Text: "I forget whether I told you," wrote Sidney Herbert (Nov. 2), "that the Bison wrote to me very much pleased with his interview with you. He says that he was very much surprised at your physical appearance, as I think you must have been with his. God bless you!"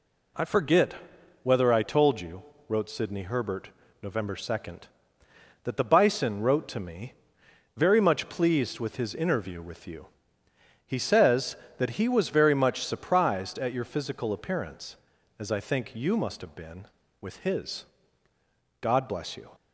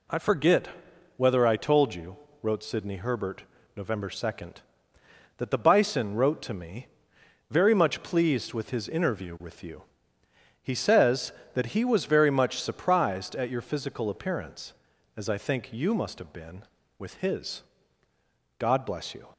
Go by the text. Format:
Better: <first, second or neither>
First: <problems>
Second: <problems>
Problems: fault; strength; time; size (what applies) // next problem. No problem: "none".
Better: neither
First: pauses between "forget" and "whether"; noticeable; at 0.9 s; 0.48 s long // pauses between "me" and "very"; noticeable; at 7.1 s; 0.64 s long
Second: pauses between "forget" and "whether"; noticeable; at 0.6 s; 0.48 s long // pauses between "me" and "very"; noticeable; at 6.8 s; 0.64 s long